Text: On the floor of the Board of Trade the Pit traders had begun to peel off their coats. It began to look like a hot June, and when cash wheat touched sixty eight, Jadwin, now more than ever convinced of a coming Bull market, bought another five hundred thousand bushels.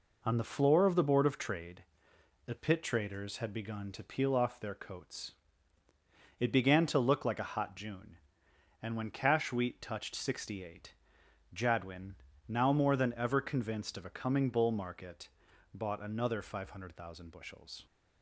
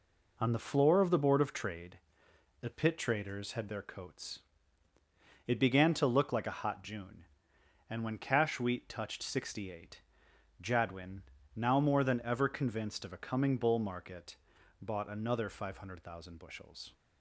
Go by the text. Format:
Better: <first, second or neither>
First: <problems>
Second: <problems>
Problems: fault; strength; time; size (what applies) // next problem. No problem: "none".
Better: first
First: pauses between "Trade" and "the"; noticeable; at 1.8 s; 0.62 s long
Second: pauses between "Trade" and "the"; noticeable; at 1.9 s; 0.62 s long // skips "begun to peel off"; at 3.6 s